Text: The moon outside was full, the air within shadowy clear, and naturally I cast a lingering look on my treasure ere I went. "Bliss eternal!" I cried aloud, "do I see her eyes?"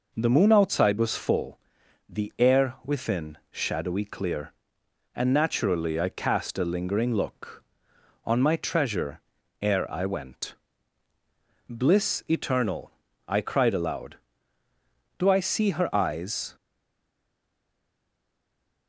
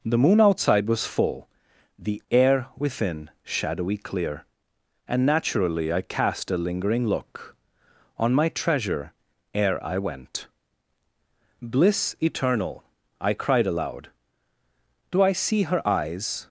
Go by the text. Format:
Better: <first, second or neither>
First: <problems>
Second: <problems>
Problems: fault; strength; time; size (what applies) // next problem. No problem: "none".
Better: second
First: pauses between "treasure" and "ere"; at 9.2 s; 0.40 s long // stays silent after the last word; from 16.5 s on; 2.3 s long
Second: pauses between "treasure" and "ere"; at 9.1 s; 0.40 s long